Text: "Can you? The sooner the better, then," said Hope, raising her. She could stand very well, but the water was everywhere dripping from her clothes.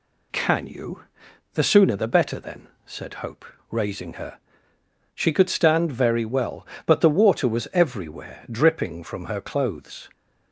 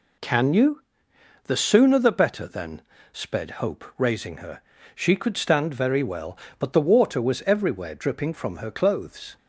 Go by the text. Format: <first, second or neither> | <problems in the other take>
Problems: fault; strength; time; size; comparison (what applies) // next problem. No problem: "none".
first | says "sped" for "said"; at 3.1 s